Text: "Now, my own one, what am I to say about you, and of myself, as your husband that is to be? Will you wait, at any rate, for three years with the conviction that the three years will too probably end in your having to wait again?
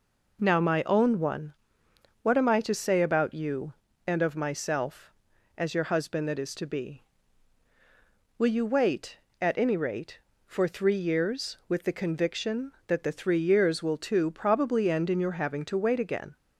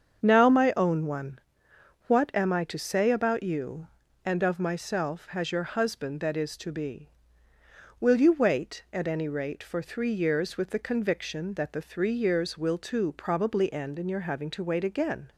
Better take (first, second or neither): first